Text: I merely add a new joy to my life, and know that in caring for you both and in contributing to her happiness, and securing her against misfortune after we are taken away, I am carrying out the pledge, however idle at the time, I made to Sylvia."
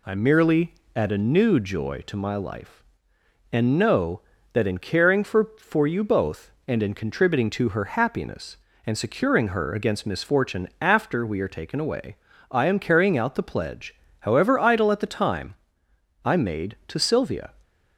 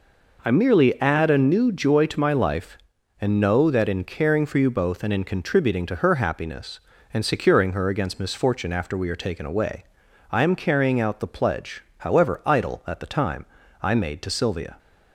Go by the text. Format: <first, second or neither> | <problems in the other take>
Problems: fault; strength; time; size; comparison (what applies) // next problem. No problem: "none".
second | pauses between "merely" and "add"; slight; at 0.7 s; 0.22 s long // says "for" twice; at 5.5 s